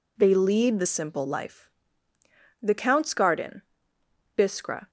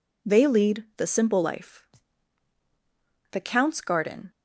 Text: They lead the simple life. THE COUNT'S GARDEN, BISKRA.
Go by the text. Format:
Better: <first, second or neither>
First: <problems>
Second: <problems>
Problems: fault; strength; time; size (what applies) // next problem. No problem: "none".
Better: first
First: none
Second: stops before "BISKRA"; at 4.3 s